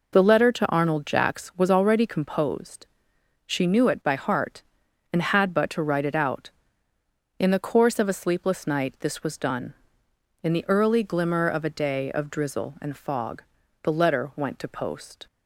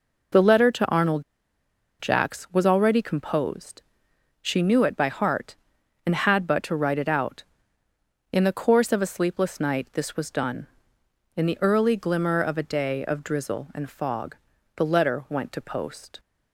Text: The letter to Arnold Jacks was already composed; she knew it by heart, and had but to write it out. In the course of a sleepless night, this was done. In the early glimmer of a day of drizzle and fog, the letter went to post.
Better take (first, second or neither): first